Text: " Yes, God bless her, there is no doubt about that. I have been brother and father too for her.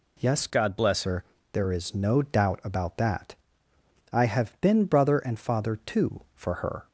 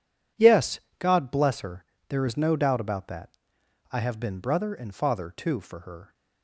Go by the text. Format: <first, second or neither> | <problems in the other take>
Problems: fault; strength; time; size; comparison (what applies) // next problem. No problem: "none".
second | changes voice from "God" to "bless"; from 0.5 to 1.0 s; 0.5 s long